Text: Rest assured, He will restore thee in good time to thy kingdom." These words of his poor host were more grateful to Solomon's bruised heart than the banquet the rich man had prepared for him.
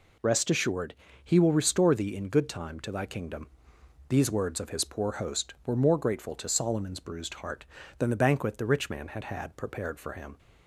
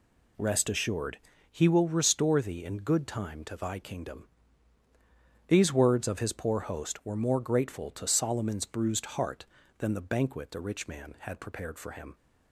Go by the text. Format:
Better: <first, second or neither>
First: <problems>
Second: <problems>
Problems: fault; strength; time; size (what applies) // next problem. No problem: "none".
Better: second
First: says "had" twice; at 9.2 s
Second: none